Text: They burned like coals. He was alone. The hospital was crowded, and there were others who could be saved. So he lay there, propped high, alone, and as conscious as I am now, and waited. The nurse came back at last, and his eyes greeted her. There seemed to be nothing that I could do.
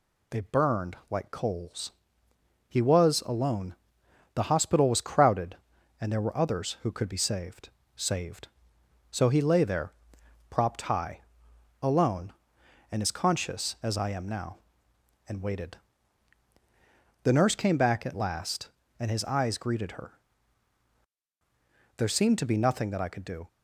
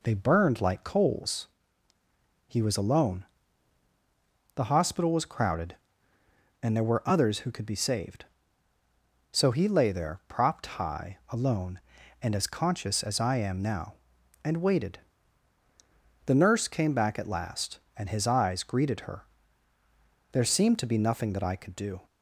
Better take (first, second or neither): second